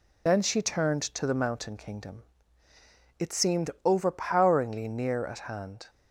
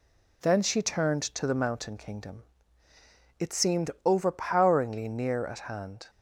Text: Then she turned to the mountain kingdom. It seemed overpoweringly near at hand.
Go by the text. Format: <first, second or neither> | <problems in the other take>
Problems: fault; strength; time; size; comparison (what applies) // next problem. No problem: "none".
second | loses the start of "Then"; at 0.2 s; 40 ms